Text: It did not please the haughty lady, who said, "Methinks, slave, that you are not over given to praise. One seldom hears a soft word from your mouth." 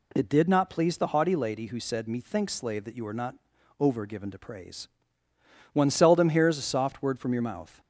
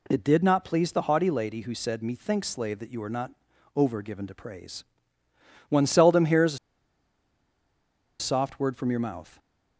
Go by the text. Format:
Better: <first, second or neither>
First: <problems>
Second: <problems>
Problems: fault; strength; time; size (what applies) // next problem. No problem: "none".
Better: first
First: pauses between "not" and "over"; at 3.3 s; 0.44 s long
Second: pauses between "not" and "over"; at 3.3 s; 0.44 s long // pauses between "a" and "soft"; strong; at 6.5 s; 1.6 s long